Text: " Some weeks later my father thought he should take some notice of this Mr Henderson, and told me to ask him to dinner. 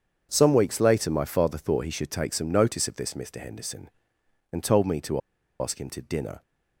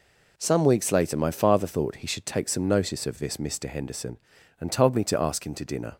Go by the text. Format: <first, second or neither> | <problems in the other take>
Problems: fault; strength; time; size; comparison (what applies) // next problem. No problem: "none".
second | starts louder than the rest; strong; until 1.3 s; 7.5 dB // pauses between "to" and "ask"; at 5.1 s; 0.40 s long